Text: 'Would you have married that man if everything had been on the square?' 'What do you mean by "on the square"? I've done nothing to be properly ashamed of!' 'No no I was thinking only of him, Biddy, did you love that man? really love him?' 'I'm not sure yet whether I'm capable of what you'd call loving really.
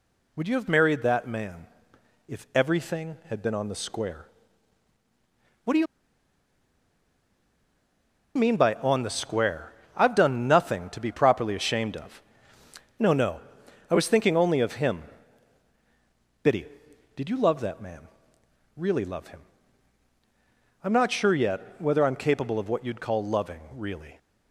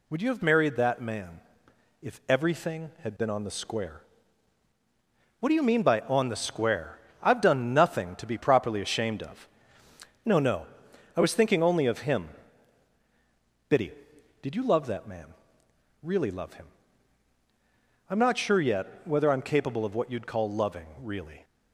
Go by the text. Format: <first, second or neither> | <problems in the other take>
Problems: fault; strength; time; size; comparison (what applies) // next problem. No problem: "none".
second | pauses between "man" and "if"; noticeable; at 1.6 s; 0.60 s long; noticeable in the second // pauses between "you" and "mean"; strong; at 5.8 s; 2.5 s long // pauses between "no" and "I"; noticeable; at 13.3 s; 0.48 s long; noticeable in the second // pauses between "loving" and "really"; slight; at 23.5 s; 0.16 s long; slight in the second